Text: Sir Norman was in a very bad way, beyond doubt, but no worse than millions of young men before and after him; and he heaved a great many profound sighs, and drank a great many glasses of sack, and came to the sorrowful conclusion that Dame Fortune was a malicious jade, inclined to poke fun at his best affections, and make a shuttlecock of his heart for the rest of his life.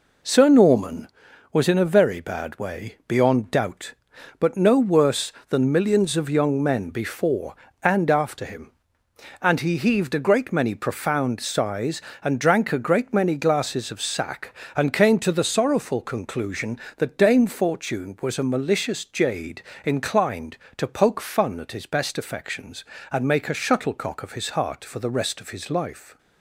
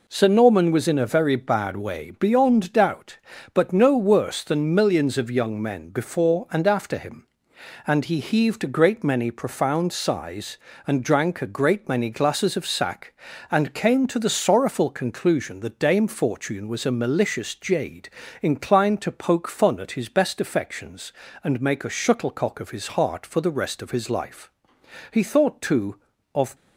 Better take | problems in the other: first | goes on to say "He thought too of"; from 25.1 s on; 1.4 s long

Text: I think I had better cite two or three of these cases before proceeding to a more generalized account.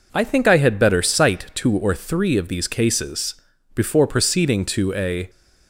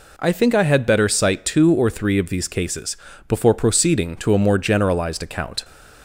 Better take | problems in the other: second | pauses between "cases" and "before"; at 3.3 s; 0.38 s long; slight in the second // stops before "more generalized account"; at 5.2 s

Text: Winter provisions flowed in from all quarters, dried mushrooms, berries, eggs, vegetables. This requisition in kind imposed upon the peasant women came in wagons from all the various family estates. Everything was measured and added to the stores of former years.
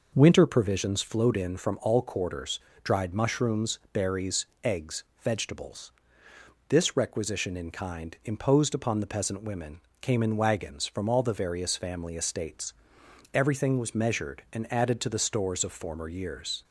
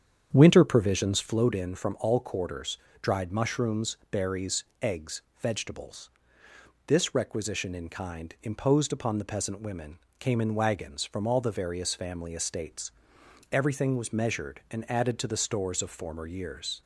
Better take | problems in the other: first | starts louder than the rest; strong; until 1.5 s; 8 dB // pauses between "women" and "came"; slight; at 9.9 s; 0.22 s long; slight in the first

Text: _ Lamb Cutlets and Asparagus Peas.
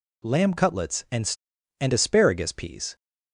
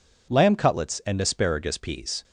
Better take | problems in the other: second | says "and" twice; at 1.8 s

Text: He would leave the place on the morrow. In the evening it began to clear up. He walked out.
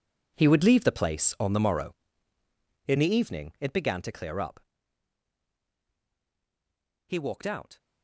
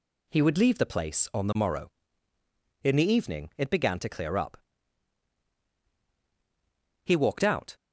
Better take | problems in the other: second | gets quieter; strong; throughout; 15 dB

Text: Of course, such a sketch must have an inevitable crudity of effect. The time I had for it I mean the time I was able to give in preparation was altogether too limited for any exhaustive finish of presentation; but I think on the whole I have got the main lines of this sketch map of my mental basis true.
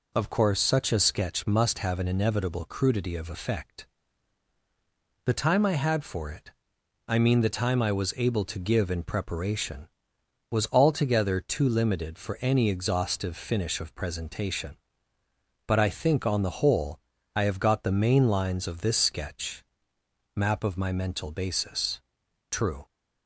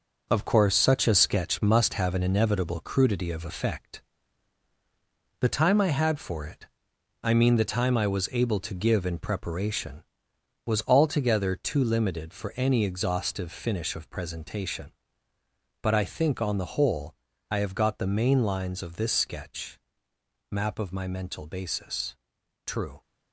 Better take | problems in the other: first | gets quieter; strong; throughout; 7.5 dB // pauses between "it" and "I"; noticeable; at 6.6 s; 0.58 s long; noticeable in the first // pauses between "whole" and "I"; slight; at 17.1 s; 0.36 s long; slight in the first // pauses between "sketch" and "map"; noticeable; at 19.7 s; 0.70 s long; noticeable in the first // pauses between "basis" and "true"; noticeable; at 22.1 s; 0.48 s long; noticeable in the first

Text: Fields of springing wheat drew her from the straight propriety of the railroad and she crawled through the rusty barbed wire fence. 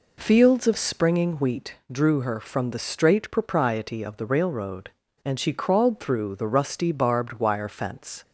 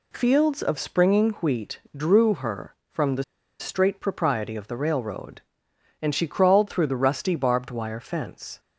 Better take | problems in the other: first | pauses between "wheat" and "drew"; slight; at 1.8 s; 0.16 s long; slight in the first // pauses between "the" and "straight"; slight; at 3.2 s; 0.35 s long

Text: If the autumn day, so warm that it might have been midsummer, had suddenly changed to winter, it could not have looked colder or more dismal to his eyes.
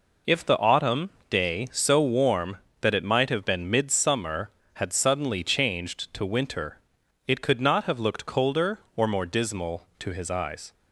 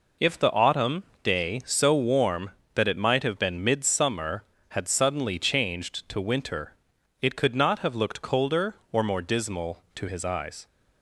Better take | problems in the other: neither | pauses between "autumn" and "day"; slight; the same in both

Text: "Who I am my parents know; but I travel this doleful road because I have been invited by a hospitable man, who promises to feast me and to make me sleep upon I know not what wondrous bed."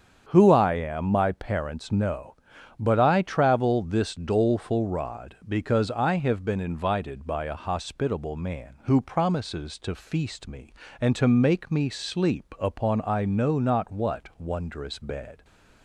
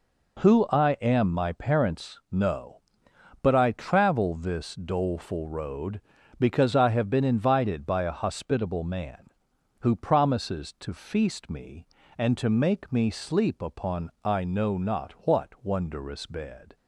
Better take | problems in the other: second | starts louder than the rest; strong; until 1.3 s; 7.5 dB // says "rod" for "road"; at 4.8 s

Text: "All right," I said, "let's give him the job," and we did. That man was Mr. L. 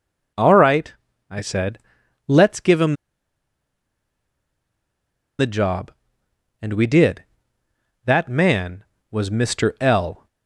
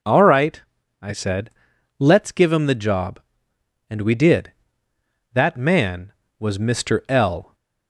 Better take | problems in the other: second | pauses between "him" and "the"; strong; at 2.9 s; 2.4 s long

